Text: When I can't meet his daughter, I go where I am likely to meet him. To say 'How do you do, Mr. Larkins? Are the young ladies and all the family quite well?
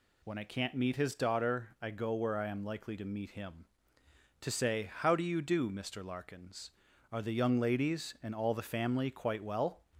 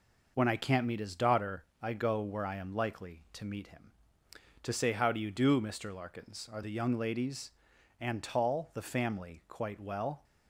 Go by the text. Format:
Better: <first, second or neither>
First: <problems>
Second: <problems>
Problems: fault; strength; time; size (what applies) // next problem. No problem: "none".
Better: first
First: none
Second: says "tall" for "all"; at 8.2 s